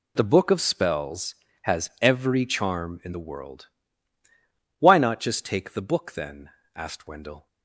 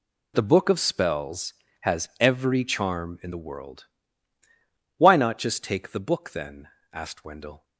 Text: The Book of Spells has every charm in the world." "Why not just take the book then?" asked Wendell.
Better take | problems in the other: neither | none

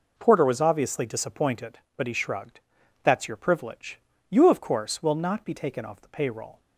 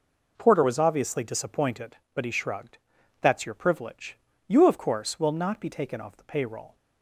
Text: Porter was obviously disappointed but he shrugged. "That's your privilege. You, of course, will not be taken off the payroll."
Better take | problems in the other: neither | none

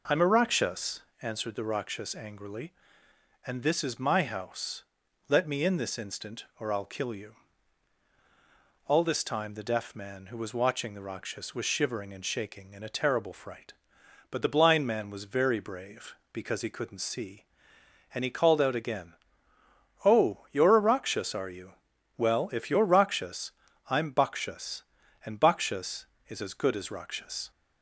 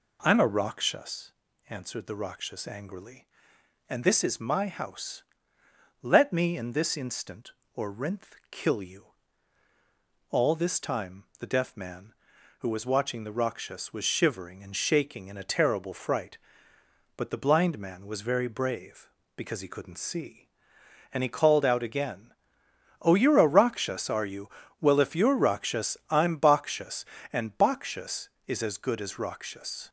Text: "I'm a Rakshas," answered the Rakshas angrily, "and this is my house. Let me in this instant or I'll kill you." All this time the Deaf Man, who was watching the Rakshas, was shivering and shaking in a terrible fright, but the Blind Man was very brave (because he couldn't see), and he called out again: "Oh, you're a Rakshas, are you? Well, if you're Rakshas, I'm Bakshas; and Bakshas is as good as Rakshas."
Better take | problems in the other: first | says "Rinth" for "I'll"; at 7.9 s

